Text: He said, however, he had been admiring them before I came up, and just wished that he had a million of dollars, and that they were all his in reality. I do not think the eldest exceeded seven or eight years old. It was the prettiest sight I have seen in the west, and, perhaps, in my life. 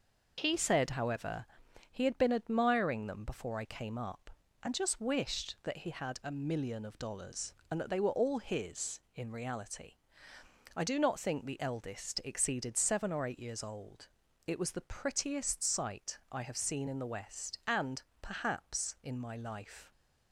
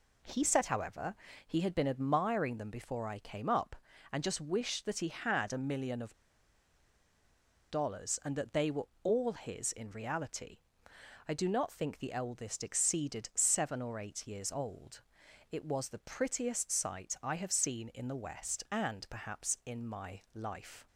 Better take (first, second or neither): first